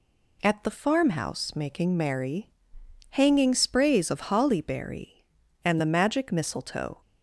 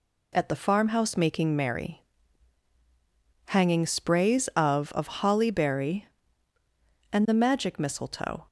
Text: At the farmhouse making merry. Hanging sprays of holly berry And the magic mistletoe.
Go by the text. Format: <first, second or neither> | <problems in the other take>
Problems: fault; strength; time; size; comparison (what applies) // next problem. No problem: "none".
first | says "of" twice; at 4.9 s